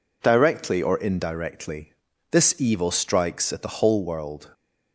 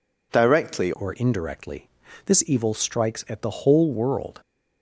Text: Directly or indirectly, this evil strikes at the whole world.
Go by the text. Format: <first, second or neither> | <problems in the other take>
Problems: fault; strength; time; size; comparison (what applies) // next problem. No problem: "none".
first | changes voice at "or"; from 0.9 s on; 3.5 s long